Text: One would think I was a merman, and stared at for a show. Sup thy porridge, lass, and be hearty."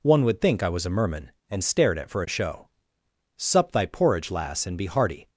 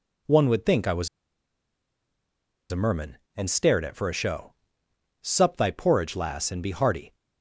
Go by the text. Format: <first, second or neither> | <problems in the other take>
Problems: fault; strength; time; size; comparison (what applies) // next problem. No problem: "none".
first | pauses between "was" and "a"; strong; at 1.0 s; 1.6 s long